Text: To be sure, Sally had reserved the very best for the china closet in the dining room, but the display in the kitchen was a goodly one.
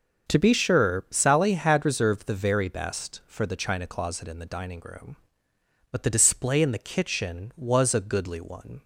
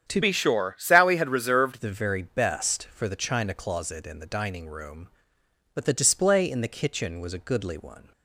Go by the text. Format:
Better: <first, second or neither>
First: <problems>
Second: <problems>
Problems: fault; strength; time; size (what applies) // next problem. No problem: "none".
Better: first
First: starts louder than the rest; until 1.4 s; 7 dB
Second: starts louder than the rest; strong; until 1.1 s; 9 dB // changes voice from "be" to "reserved"; from 0.2 to 1.8 s; 1.6 s long